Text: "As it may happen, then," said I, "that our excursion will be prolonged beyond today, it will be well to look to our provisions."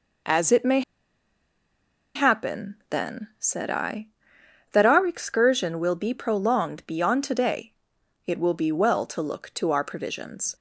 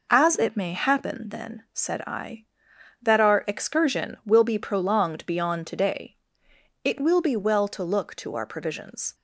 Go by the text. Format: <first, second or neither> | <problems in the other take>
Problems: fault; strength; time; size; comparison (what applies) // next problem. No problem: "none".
second | pauses between "may" and "happen"; strong; at 0.8 s; 1.3 s long